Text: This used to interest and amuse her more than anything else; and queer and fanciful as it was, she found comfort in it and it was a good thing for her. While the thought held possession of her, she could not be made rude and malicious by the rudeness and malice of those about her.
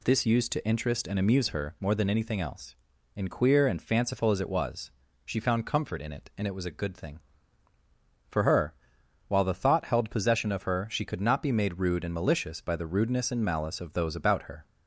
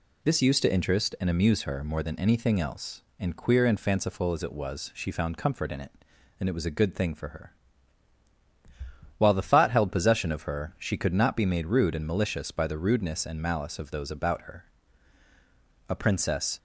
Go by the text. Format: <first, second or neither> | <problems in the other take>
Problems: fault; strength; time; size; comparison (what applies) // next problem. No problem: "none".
first | goes on to say "A princess"; noticeable; from 15.8 s on; 0.70 s long